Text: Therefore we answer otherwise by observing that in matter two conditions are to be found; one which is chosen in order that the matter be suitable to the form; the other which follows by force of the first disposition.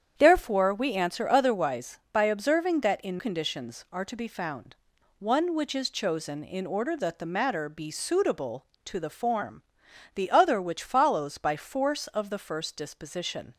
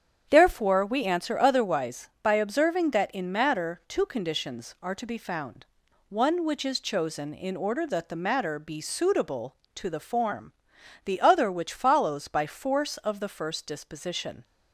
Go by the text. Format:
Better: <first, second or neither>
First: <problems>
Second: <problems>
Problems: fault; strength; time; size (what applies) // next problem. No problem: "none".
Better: second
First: starts louder than the rest; strong; until 1.1 s; 8.5 dB // skips "matter two"; at 3.1 s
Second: starts louder than the rest; strong; until 1.3 s; 8.5 dB